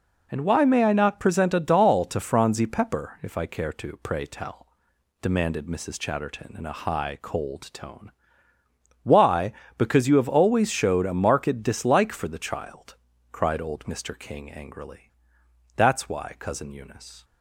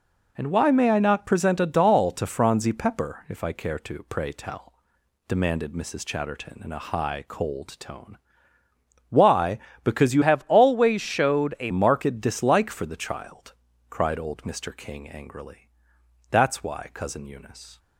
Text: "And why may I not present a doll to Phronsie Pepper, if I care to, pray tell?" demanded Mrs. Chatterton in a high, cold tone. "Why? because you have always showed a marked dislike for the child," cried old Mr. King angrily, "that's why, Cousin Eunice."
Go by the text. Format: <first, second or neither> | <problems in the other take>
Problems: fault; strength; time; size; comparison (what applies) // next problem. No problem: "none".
first | changes voice from "have" to "a"; from 10.2 to 11.7 s; 1.5 s long